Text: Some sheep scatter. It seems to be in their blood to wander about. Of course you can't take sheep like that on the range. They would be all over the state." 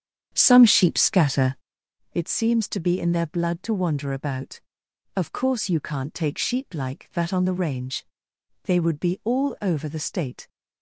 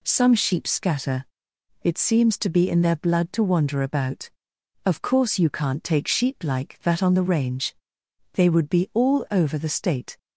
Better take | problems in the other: second | starts louder than the rest; strong; until 1.9 s; 8.5 dB

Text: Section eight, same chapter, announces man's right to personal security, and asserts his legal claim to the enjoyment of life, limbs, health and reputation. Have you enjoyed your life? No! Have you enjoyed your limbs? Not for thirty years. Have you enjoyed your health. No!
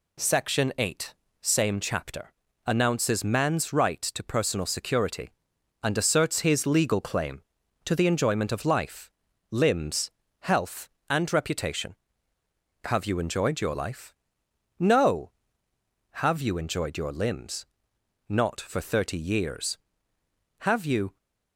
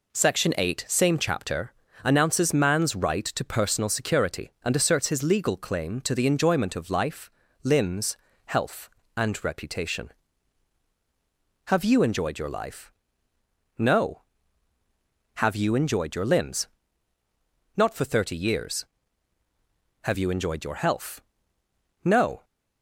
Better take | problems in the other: second | stops before "enjoyed your health No"; at 21.1 s

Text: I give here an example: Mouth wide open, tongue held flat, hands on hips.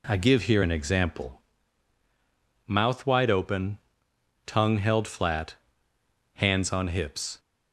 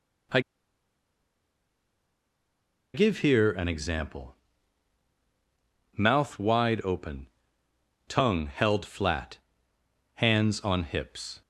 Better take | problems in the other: first | pauses between "I" and "give"; strong; at 0.3 s; 2.5 s long

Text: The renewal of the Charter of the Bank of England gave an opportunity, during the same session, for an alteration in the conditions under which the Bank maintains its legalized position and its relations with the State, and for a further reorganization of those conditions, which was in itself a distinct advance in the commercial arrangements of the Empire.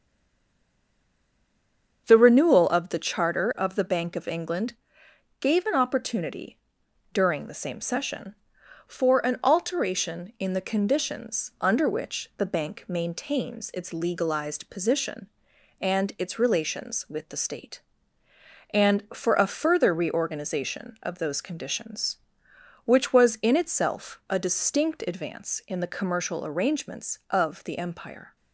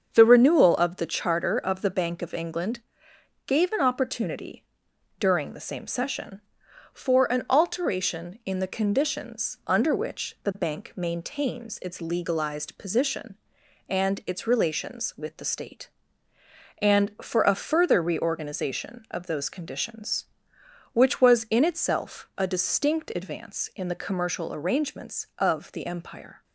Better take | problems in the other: second | stays silent before the first word; noticeable; until 2.0 s; 2.0 s long // starts louder than the rest; until 3.0 s; 7 dB; also in the second // pauses between "England" and "gave"; noticeable; at 4.7 s; 0.66 s long; noticeable in the second

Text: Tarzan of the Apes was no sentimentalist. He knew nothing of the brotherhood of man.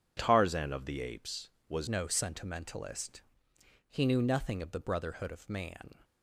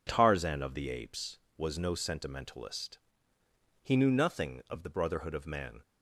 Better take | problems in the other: second | changes voice at "no"; from 1.8 s on; 4.1 s long

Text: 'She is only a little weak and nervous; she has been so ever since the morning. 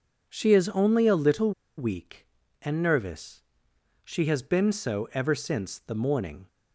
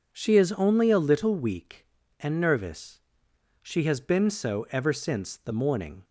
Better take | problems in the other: second | pauses between "little" and "weak"; slight; at 1.5 s; 0.26 s long

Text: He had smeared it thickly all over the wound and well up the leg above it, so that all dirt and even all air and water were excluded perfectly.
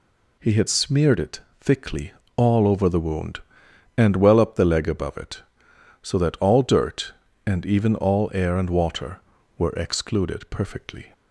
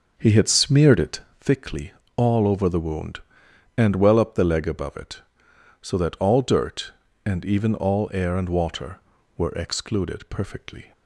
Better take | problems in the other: first | starts louder than the rest; until 1.6 s; 6.5 dB // pauses between "it" and "thickly"; slight; at 1.2 s; 0.20 s long; slight in the first // pauses between "thickly" and "all"; slight; at 1.9 s; 0.24 s long; slight in the first

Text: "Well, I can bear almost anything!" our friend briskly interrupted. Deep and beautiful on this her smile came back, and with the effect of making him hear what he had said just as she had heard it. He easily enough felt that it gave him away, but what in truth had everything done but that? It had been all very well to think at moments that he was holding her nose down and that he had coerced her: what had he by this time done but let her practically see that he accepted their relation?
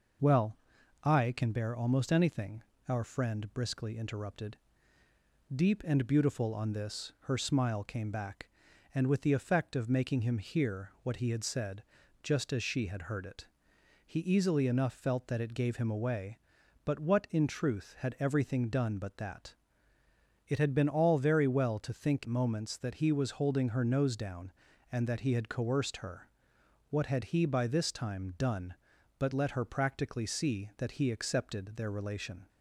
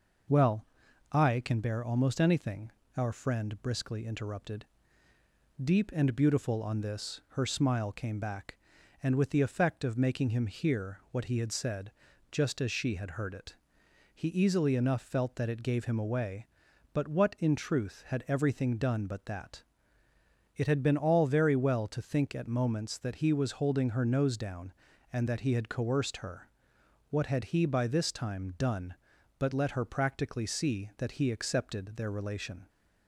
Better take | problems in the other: second | pauses between "said" and "just"; at 11.8 s; 0.40 s long; also in the second // skips "at"; at 22.2 s

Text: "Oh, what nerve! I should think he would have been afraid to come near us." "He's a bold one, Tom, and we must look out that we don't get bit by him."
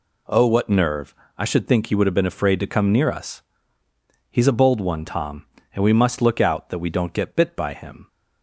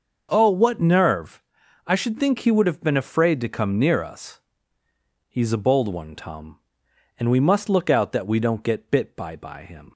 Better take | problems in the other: first | starts louder than the rest; until 1.3 s; 6.5 dB // says "by" twice; at 9.3 s

